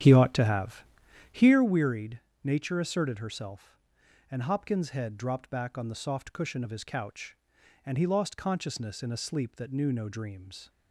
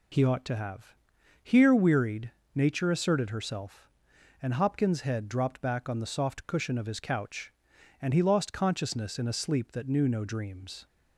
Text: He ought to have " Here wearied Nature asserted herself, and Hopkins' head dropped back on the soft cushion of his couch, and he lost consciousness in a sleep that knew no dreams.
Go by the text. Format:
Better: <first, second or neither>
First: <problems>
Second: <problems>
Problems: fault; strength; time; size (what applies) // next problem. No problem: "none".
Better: second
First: starts louder than the rest; strong; until 1.6 s; 8 dB // pauses between "wearied" and "Nature"; slight; at 2.2 s; 0.22 s long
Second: pauses between "wearied" and "Nature"; slight; at 2.3 s; 0.22 s long